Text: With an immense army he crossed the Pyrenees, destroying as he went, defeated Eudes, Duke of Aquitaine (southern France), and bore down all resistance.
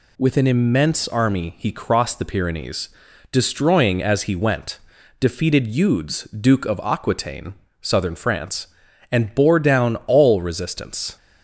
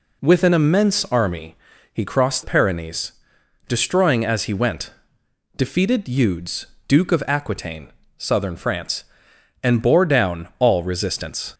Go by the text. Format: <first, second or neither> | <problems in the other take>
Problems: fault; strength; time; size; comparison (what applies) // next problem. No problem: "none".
first | pauses between "army" and "he"; at 1.5 s; 0.38 s long // skips "the"; at 2.4 s